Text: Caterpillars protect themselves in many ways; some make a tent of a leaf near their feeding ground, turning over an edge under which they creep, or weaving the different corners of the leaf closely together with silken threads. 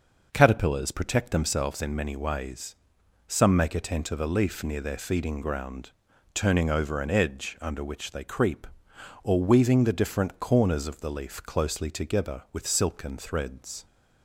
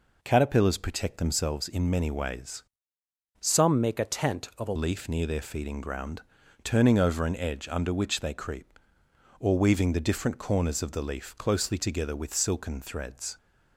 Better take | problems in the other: first | changes voice from "some" to "a"; from 3.4 to 4.7 s; 1.3 s long

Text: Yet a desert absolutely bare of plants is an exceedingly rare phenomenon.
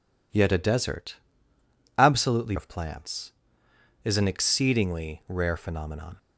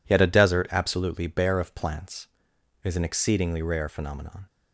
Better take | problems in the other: second | pauses between "desert" and "absolutely"; noticeable; at 1.1 s; 0.82 s long // skips "bare"; at 2.5 s

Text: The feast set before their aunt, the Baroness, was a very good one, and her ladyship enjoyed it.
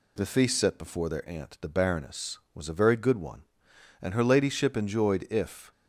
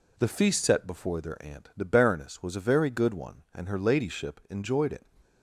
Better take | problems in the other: second | says "if" for "it"; at 5.2 s

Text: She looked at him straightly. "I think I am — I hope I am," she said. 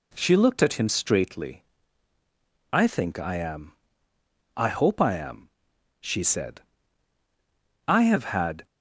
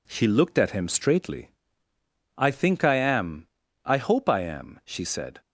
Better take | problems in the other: second | goes on to say "I have had"; noticeable; from 7.8 s on; 0.78 s long

